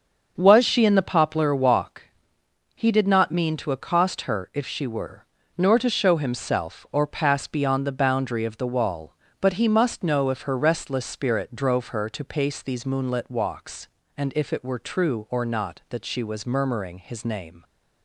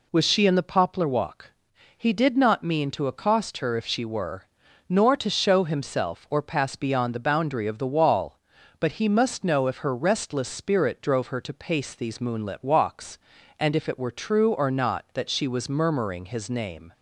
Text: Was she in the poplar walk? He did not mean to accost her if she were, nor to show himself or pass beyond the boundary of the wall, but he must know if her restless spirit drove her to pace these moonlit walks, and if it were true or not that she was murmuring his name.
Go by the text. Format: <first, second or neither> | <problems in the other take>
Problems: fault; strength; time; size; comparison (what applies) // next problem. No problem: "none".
second | starts louder than the rest; until 2.0 s; 6.5 dB